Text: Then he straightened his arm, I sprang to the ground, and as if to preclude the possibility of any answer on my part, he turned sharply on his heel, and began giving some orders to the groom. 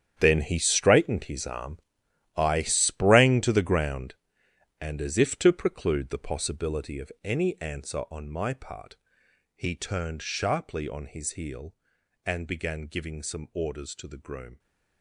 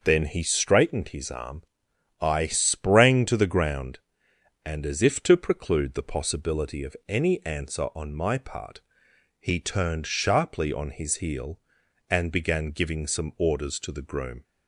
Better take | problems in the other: second | gets quieter; strong; throughout; 14 dB

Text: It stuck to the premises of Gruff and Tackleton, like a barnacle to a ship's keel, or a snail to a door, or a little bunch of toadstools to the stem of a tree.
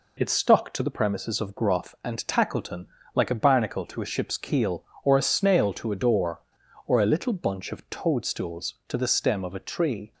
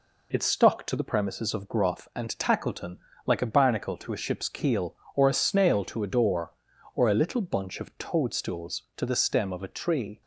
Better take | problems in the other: neither | none

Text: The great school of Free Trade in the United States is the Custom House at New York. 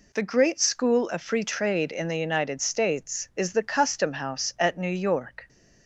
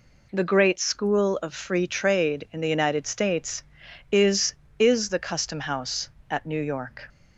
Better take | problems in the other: first | says "is" twice; at 4.7 s

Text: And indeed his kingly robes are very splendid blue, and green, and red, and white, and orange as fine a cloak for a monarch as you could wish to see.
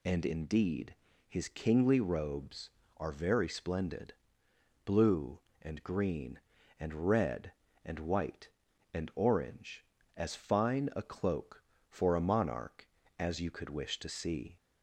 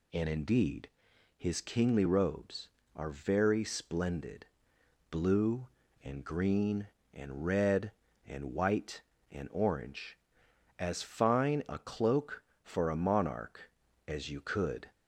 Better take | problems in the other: first | pauses between "indeed" and "his"; noticeable; at 0.8 s; 0.48 s long; slight in the first // pauses between "splendid" and "blue"; noticeable; at 4.4 s; 0.64 s long; noticeable in the first // stops before "wish to see"; at 14.9 s

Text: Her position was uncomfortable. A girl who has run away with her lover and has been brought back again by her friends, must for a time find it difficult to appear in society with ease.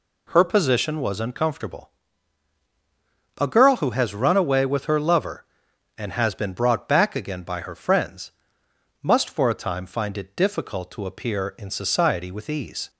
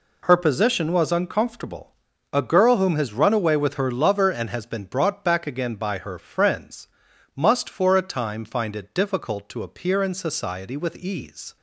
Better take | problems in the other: first | says "whom" for "who"; at 2.7 s

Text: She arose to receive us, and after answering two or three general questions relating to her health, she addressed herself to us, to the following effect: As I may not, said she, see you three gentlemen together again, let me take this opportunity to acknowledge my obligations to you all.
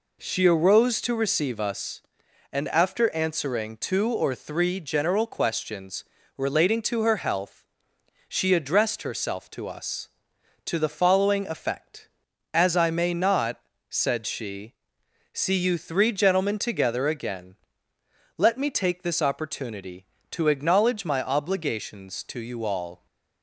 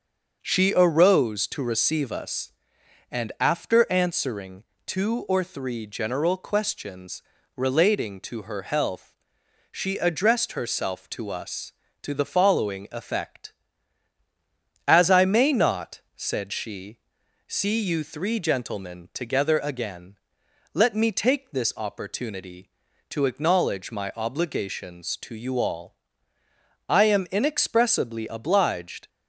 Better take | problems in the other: first | starts louder than the rest; noticeable; until 1.4 s; 6 dB // pauses between "answering" and "two"; slight; at 4.6 s; 0.22 s long // pauses between "questions" and "relating"; slight; at 7.2 s; 0.34 s long; slight in the first // goes on to say "I am inexpressibly obliged"; strong; from 26.8 s on; 2.2 s long

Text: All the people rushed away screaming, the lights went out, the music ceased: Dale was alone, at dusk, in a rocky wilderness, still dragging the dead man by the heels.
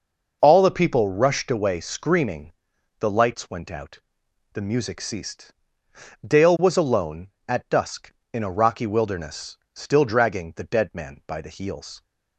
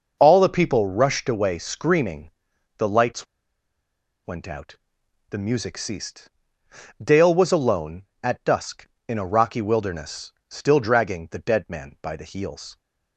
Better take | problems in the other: first | pauses between "lights" and "went"; at 3.2 s; 1.0 s long

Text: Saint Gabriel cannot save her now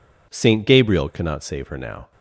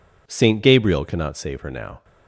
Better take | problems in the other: neither | none

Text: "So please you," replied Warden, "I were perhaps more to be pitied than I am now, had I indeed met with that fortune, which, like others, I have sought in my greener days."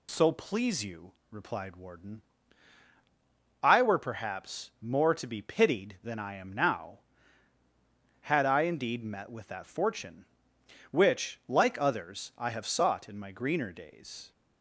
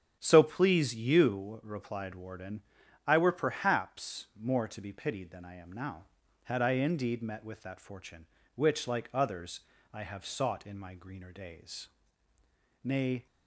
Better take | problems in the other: first | starts louder than the rest; strong; until 1.2 s; 8 dB // goes on to say "Nay"; slight; from 12.8 s on; 0.44 s long

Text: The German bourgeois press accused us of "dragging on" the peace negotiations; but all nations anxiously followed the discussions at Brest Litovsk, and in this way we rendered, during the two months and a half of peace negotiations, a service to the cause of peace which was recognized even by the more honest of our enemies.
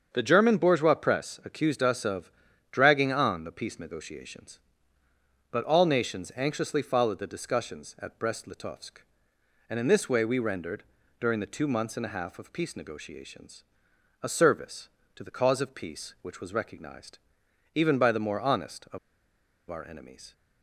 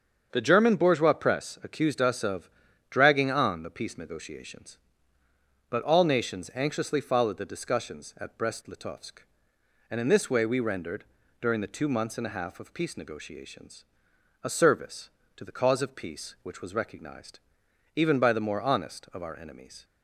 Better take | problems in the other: second | starts louder than the rest; strong; until 1.1 s; 7 dB; strong in the second // pauses between "of" and "dragging"; at 2.3 s; 0.38 s long; also in the second // pauses between "recognized" and "even"; noticeable; at 17.1 s; 0.56 s long; noticeable in the second // pauses between "of" and "our"; noticeable; at 18.9 s; 0.72 s long

